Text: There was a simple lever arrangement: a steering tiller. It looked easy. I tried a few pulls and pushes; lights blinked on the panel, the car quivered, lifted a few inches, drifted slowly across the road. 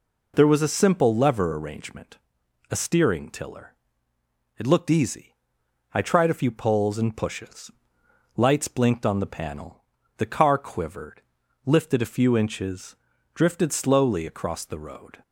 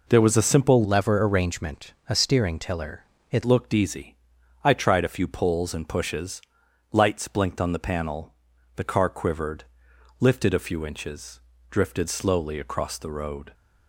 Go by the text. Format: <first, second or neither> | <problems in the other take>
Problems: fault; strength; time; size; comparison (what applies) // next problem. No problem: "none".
first | changes voice from "lever" to "It"; from 0.8 to 3.4 s; 2.6 s long